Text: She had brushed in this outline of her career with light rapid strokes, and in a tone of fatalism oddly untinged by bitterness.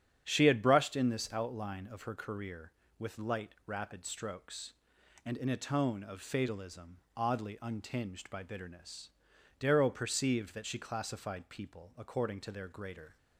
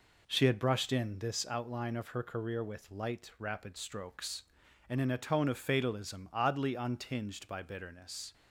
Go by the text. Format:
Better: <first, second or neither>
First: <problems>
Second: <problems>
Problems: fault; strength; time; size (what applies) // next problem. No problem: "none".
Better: second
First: starts louder than the rest; strong; until 1.2 s; 9 dB // pauses between "fatalism" and "oddly"; slight; at 6.9 s; 0.18 s long // goes on to say "Darrow perceived that she classified people according to their greater"; strong; from 9.5 s on; 3.5 s long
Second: none